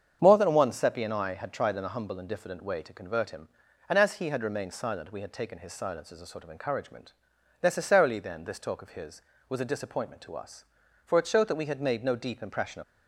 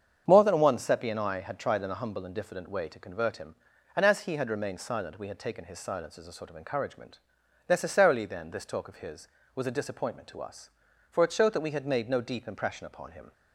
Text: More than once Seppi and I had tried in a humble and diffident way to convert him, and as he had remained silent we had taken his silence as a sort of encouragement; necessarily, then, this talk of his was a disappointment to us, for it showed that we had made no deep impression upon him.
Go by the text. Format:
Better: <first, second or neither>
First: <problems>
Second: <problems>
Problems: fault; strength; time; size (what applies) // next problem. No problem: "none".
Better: second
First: starts louder than the rest; strong; until 1.2 s; 7.5 dB // stops before "upon him"; at 12.8 s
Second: starts louder than the rest; strong; until 1.2 s; 7.5 dB